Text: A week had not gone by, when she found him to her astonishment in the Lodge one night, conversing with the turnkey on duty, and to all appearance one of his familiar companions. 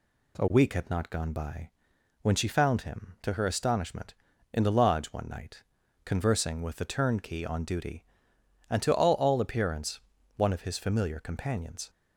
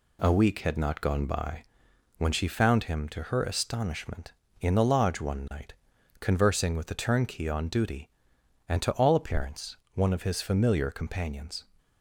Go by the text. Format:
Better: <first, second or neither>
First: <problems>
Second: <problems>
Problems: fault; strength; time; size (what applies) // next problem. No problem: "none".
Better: second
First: says "all" twice; at 9.1 s // pauses between "appearance" and "one"; slight; at 9.9 s; 0.36 s long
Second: pauses between "appearance" and "one"; slight; at 9.7 s; 0.20 s long